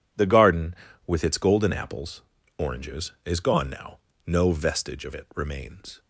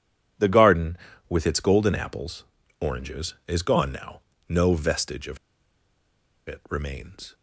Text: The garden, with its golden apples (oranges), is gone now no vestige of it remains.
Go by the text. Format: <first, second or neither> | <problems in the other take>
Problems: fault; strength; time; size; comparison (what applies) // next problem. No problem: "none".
first | pauses between "now" and "no"; slight; at 4.1 s; 0.30 s long; slight in the first // pauses between "of" and "it"; at 5.3 s; 1.1 s long